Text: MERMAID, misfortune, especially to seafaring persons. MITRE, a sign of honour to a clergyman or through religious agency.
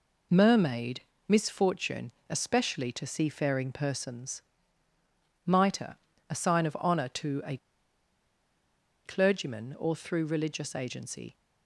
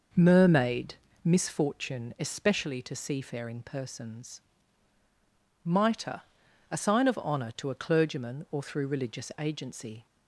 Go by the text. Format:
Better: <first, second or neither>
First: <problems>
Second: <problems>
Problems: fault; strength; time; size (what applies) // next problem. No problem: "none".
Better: second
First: pauses between "a" and "clergyman"; strong; at 7.5 s; 1.4 s long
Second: none